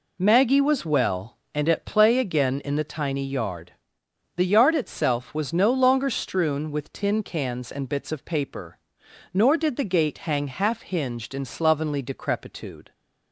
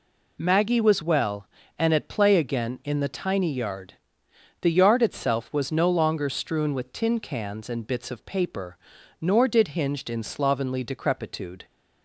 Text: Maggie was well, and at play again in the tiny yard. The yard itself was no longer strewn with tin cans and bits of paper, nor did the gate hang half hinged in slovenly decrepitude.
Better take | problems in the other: first | skips "the gate hang half"; at 9.6 s

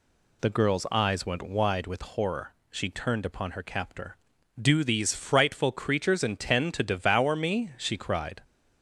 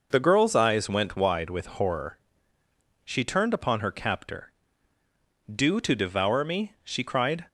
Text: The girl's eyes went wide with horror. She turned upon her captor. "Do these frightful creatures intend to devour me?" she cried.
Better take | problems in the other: first | skips "these frightful creatures intend"; at 5.7 s

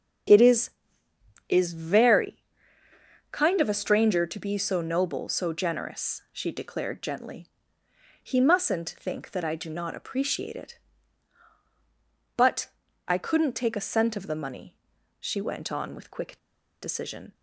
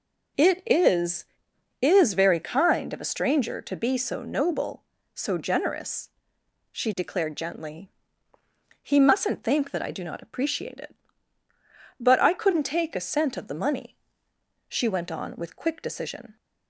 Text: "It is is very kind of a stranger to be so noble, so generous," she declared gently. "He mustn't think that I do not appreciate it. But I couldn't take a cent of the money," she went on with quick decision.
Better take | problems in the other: second | starts louder than the rest; strong; until 2.0 s; 7 dB // pauses between "very" and "kind"; noticeable; at 2.4 s; 0.86 s long // pauses between "But" and "I"; at 12.6 s; 0.40 s long // pauses between "quick" and "decision"; noticeable; at 16.3 s; 0.46 s long

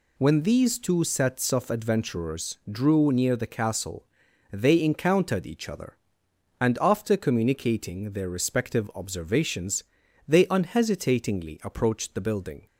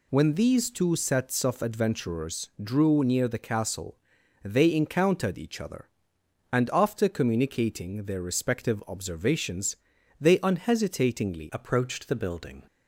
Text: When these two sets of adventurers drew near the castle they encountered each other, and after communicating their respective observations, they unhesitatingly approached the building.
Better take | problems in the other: first | pauses between "castle" and "they"; noticeable; at 3.9 s; 0.46 s long; noticeable in the first // changes voice at "approached"; from 11.5 s on; 1.1 s long

